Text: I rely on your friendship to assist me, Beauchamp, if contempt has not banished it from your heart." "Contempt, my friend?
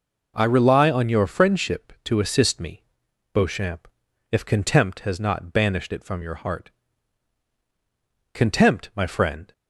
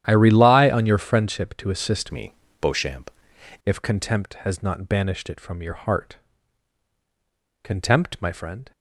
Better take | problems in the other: first | starts louder than the rest; strong; until 1.0 s; 10.5 dB // changes voice from "me" to "Beauchamp"; from 2.1 to 3.1 s; 1.0 s long

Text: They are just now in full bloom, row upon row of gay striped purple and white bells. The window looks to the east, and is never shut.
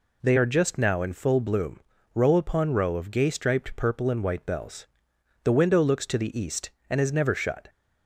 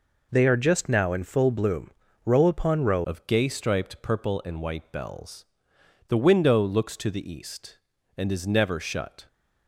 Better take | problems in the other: first | changes voice at "of"; from 3.0 s on; 6.2 s long

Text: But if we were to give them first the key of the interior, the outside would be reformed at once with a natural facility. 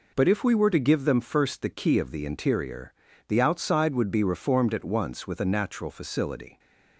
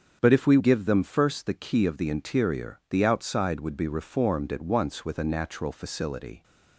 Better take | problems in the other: first | starts louder than the rest; strong; until 1.2 s; 7.5 dB // skips "were to"; at 0.5 s

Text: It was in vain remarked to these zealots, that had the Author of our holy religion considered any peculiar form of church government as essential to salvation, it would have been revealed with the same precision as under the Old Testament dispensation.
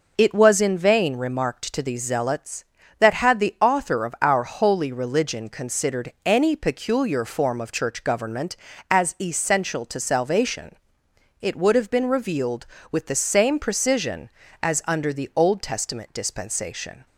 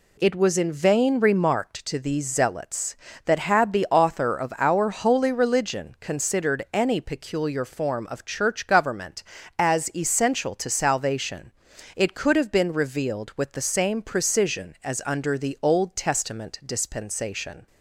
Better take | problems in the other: first | says "could" for "would"; at 12.1 s

